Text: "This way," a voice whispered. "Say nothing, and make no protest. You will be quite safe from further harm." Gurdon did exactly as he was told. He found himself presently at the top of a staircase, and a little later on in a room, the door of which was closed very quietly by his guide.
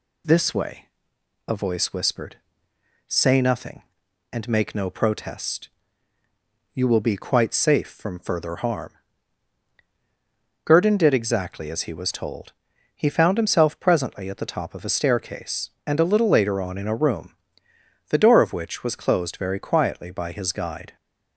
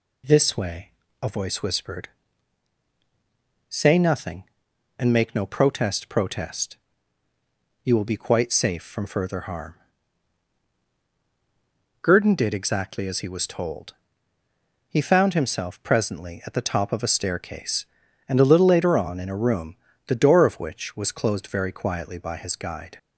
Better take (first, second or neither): first